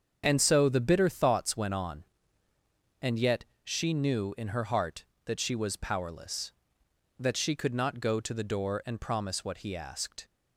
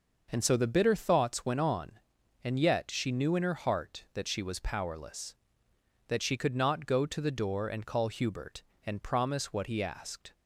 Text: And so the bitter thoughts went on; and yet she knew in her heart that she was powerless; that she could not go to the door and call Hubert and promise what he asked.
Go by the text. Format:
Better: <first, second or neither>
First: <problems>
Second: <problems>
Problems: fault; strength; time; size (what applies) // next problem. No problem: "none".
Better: second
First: starts louder than the rest; strong; until 1.2 s; 7 dB // pauses between "yet" and "she"; slight; at 3.4 s; 0.18 s long // skips "and call Hubert"; at 8.8 s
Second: none